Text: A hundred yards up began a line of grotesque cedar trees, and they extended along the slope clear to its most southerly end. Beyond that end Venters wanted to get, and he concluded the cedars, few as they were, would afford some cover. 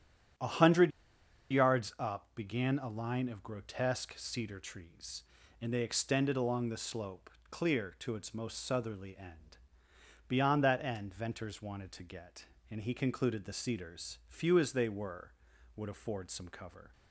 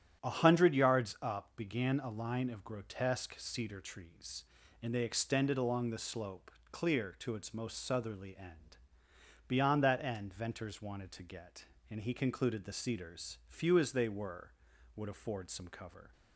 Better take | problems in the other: second | starts louder than the rest; strong; until 2.0 s; 9 dB; strong in the second // pauses between "hundred" and "yards"; noticeable; at 0.9 s; 0.61 s long // pauses between "slope" and "clear"; slight; at 7.2 s; 0.22 s long; slight in the second

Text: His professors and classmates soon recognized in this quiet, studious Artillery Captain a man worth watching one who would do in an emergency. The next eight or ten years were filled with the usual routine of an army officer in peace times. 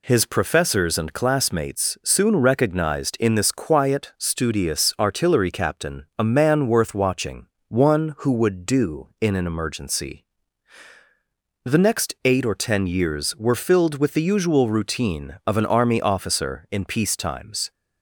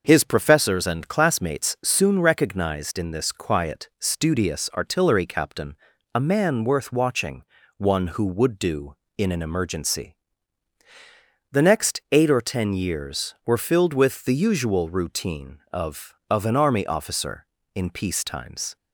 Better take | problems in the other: first | starts louder than the rest; noticeable; until 1.0 s; 6 dB // pauses between "Captain" and "a"; at 5.7 s; 0.40 s long // pauses between "watching" and "one"; slight; at 7.4 s; 0.36 s long; slight in the first // says "of" twice; at 16.2 s

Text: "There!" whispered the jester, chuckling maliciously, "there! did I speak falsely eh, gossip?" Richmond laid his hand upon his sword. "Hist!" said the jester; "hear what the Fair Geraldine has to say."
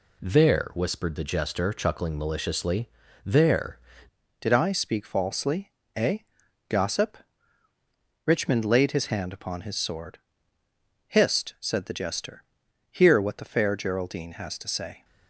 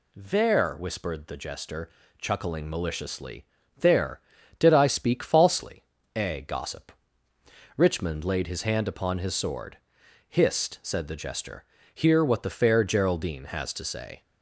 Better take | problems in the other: second | changes voice at "did"; from 4.4 s on; 10.6 s long // pauses between "falsely" and "eh"; slight; at 5.7 s; 0.24 s long; slight in the second

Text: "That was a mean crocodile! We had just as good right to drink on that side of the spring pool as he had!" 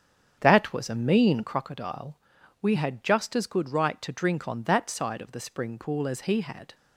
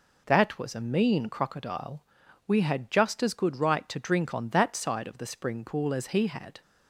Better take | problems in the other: second | starts louder than the rest; strong; until 1.5 s; 7.5 dB

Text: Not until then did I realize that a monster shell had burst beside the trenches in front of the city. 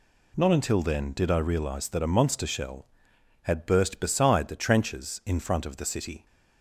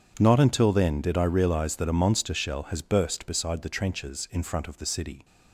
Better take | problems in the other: first | starts louder than the rest; strong; until 1.1 s; 8 dB // says "has" for "had"; at 2.6 s

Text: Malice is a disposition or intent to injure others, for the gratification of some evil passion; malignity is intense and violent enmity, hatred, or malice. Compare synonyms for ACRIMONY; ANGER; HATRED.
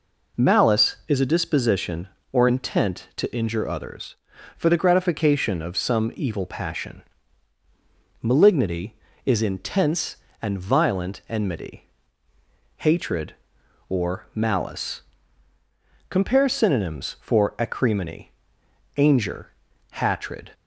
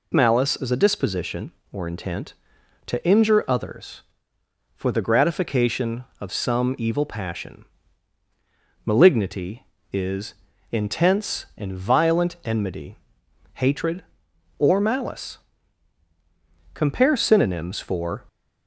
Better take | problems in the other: first | pauses between "is" and "intense"; slight; at 10.3 s; 0.36 s long // stops before "ACRIMONY ANGER HATRED"; at 18.2 s

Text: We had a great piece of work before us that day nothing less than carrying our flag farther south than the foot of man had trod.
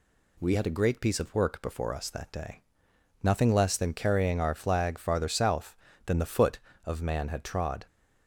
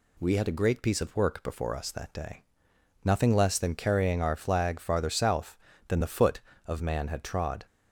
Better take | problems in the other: neither | pauses between "day" and "nothing"; noticeable; the same in both

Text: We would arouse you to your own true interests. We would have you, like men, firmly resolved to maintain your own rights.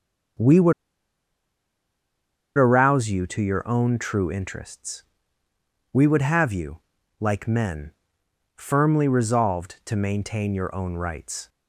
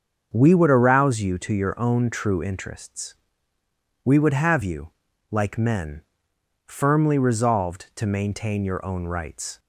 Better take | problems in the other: second | starts louder than the rest; until 3.2 s; 6.5 dB; also in the second // pauses between "would" and "arouse"; strong; at 0.7 s; 1.8 s long

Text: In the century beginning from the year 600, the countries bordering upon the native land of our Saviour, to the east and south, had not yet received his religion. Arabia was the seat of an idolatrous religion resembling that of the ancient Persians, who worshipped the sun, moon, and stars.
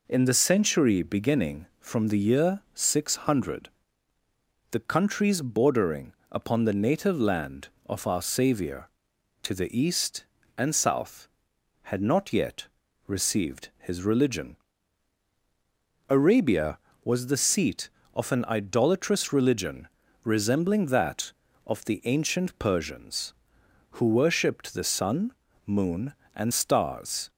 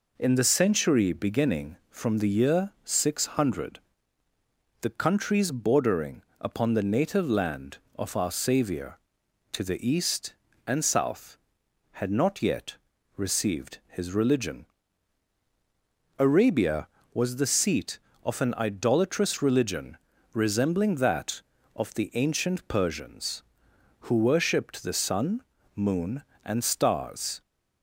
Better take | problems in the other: neither | pauses between "bordering" and "upon"; slight; the same in both // pauses between "yet" and "received"; the same in both // pauses between "religion" and "resembling"; slight; the same in both

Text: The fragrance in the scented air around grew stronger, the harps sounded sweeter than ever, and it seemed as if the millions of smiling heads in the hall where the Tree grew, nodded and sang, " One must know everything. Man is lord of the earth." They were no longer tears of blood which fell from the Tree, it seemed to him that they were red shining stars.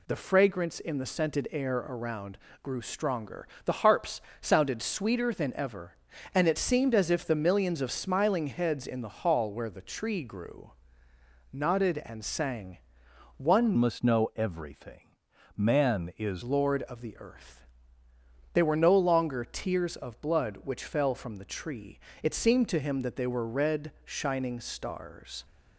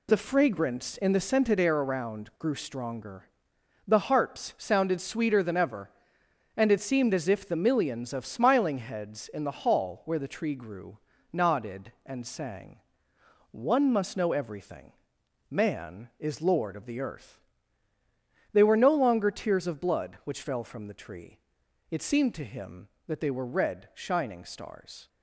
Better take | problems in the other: second | pauses between "around" and "grew"; slight; at 2.3 s; 0.24 s long // pauses between "harps" and "sounded"; slight; at 4.2 s; 0.18 s long // changes voice from "must" to "is"; from 13.7 to 16.4 s; 2.7 s long

